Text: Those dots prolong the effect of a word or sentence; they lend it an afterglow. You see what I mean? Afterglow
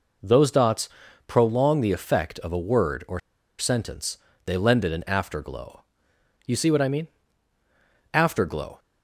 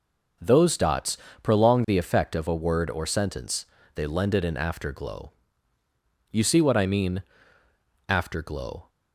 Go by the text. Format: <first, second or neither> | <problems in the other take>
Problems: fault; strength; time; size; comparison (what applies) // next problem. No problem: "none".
second | pauses between "dots" and "prolong"; at 0.8 s; 0.38 s long; slight in the second // pauses between "or" and "sentence"; at 3.1 s; 0.40 s long